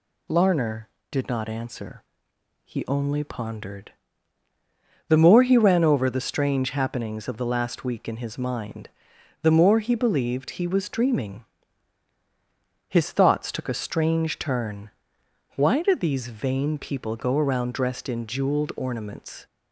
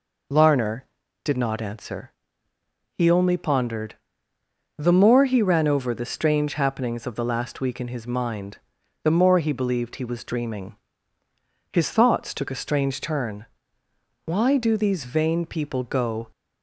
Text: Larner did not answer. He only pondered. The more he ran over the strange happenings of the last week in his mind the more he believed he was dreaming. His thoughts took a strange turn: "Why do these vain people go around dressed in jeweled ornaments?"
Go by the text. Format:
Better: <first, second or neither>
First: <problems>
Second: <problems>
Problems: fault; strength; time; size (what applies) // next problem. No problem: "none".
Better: first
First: pauses between "mind" and "the"; noticeable; at 8.8 s; 0.54 s long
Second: pauses between "mind" and "the"; noticeable; at 8.5 s; 0.46 s long // stops before "around dressed in jeweled ornaments"; at 16.3 s